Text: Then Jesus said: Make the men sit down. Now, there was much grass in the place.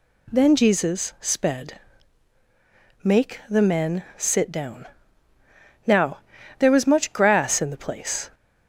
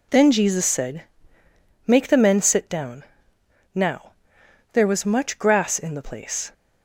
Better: second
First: says "sped" for "said"; at 1.2 s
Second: none

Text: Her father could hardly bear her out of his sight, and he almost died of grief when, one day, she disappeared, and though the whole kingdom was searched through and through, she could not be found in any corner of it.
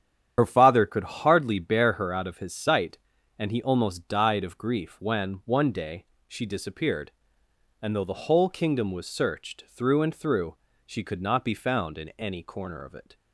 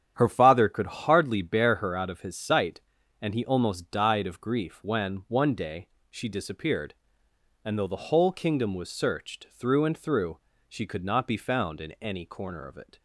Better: second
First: loses the start of "Her"; at 0.3 s; 55 ms // starts louder than the rest; strong; until 1.3 s; 9.5 dB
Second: starts louder than the rest; strong; until 1.1 s; 9 dB

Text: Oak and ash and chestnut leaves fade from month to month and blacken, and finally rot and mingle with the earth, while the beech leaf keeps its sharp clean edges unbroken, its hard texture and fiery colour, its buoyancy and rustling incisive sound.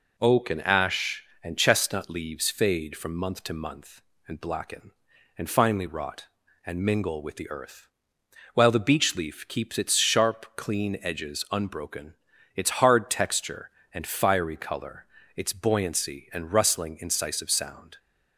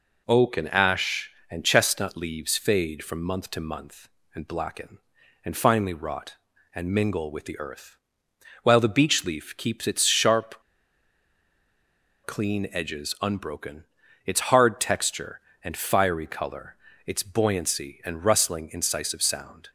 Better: first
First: none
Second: pauses between "sharp" and "clean"; strong; at 10.6 s; 1.6 s long

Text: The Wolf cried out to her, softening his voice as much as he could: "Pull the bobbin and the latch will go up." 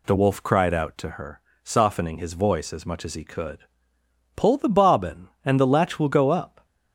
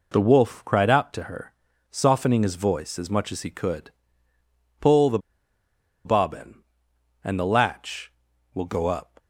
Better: first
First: none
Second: pauses between "the" and "bobbin"; noticeable; at 5.1 s; 0.86 s long

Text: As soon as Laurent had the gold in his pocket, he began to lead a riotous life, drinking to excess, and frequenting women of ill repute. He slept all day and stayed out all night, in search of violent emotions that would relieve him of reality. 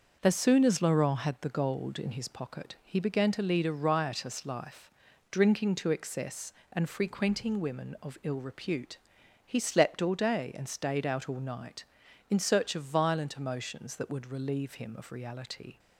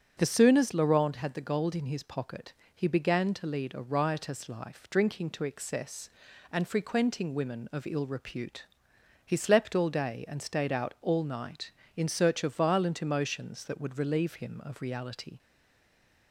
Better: first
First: starts louder than the rest; noticeable; until 1.2 s; 6 dB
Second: starts louder than the rest; strong; until 1.2 s; 8.5 dB // stays silent after the last word; slight; from 15.3 s on; 1.0 s long

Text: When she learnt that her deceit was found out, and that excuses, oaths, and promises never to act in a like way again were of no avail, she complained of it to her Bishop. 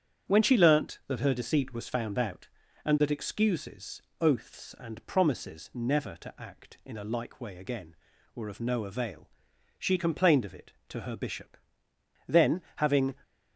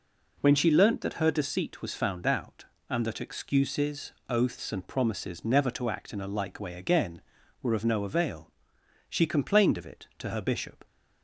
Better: second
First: starts louder than the rest; strong; until 1.3 s; 8.5 dB // goes on to say "Then having"; noticeable; from 12.2 s on; 0.88 s long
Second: none

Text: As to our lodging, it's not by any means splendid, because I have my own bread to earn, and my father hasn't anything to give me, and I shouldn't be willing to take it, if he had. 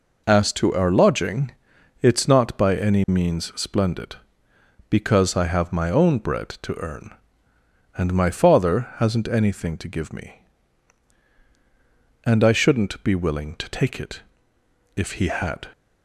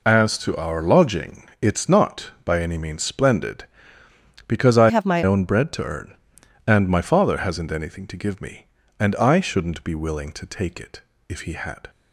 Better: first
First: none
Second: changes voice from "have" to "my"; from 4.8 to 5.2 s; 0.4 s long

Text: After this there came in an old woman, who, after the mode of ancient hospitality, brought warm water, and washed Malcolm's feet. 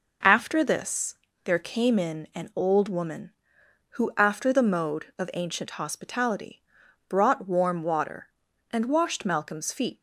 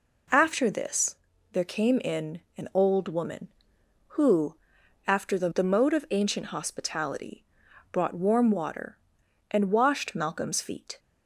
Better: first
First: pauses between "this" and "there"; slight; at 1.1 s; 0.30 s long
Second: pauses between "this" and "there"; at 1.1 s; 0.38 s long // pauses between "in" and "an"; slight; at 2.4 s; 0.16 s long // says "the" twice; at 5.4 s

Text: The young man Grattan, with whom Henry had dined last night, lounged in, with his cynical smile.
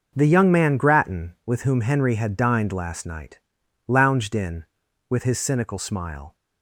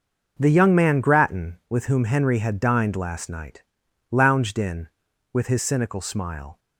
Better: neither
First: none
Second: none

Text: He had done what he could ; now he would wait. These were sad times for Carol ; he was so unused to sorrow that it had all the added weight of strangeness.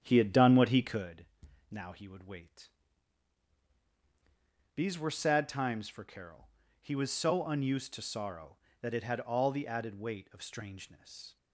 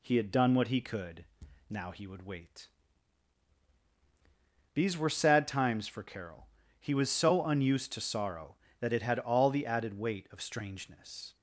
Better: second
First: starts louder than the rest; strong; until 1.1 s; 9 dB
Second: none

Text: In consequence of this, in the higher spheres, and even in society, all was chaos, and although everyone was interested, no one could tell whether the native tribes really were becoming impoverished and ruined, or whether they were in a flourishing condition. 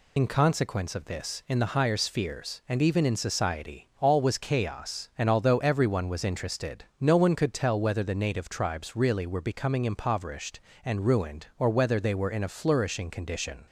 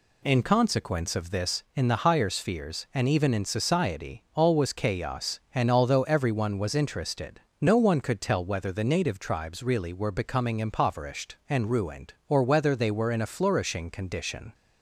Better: second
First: loses the start of "In"; at 0.1 s; 65 ms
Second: none

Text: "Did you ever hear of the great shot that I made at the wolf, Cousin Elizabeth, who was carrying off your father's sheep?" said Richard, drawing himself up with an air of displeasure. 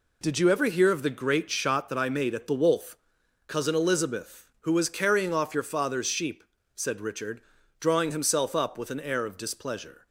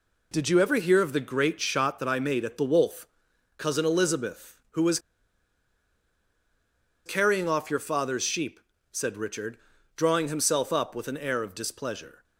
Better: first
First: none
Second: pauses between "was" and "carrying"; strong; at 4.9 s; 2.0 s long

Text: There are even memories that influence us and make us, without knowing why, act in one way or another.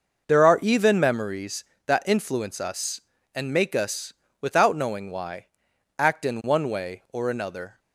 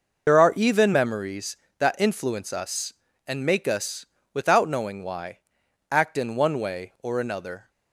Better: first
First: none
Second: loses the start of "There"; at 0.2 s; 65 ms

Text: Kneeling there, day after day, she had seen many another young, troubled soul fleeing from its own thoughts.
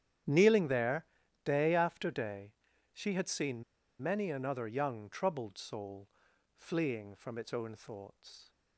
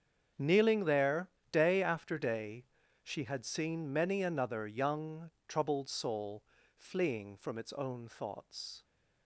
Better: second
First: starts louder than the rest; strong; until 1.6 s; 10 dB // pauses between "seen" and "many"; at 3.6 s; 0.38 s long // pauses between "soul" and "fleeing"; noticeable; at 6.0 s; 0.46 s long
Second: starts louder than the rest; strong; until 1.5 s; 7 dB // pauses between "soul" and "fleeing"; slight; at 6.4 s; 0.34 s long

